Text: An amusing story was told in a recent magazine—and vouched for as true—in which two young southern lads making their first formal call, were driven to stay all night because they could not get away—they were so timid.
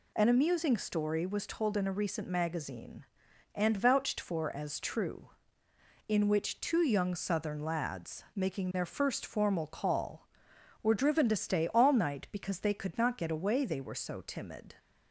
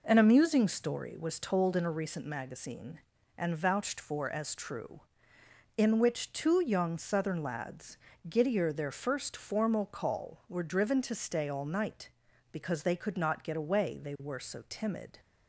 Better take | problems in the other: first | says "giddier" for "making"; at 8.2 s

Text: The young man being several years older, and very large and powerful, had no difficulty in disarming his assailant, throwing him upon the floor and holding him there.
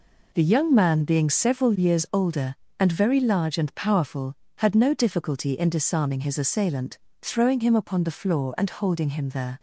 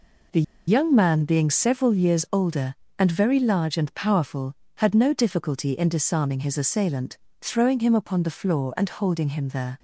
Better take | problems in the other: first | pauses between "The" and "young"; slight; at 0.4 s; 0.25 s long

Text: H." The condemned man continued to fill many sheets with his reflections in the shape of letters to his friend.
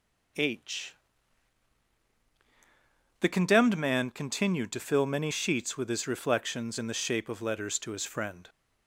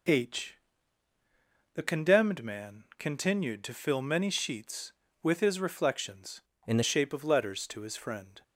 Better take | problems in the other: first | changes voice from "in" to "the"; from 6.6 to 6.8 s; 0.2 s long

